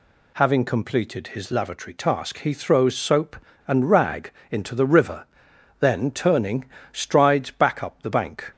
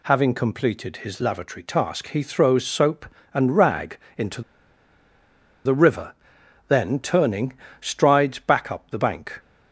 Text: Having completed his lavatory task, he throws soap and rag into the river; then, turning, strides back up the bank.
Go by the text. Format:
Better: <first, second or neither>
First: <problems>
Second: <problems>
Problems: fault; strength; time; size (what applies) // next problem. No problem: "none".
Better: first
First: pauses between "rag" and "into"; slight; at 4.3 s; 0.20 s long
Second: pauses between "rag" and "into"; slight; at 3.9 s; 0.20 s long // pauses between "into" and "the"; at 4.4 s; 1.2 s long